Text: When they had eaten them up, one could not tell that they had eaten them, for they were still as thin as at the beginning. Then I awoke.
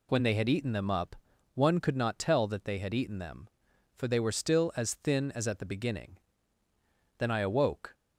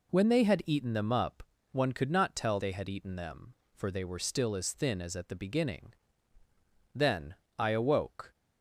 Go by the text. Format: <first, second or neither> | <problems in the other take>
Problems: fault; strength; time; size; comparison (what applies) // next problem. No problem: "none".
first | skips "that"; at 2.5 s // pauses between "Then" and "I"; slight; at 7.3 s; 0.24 s long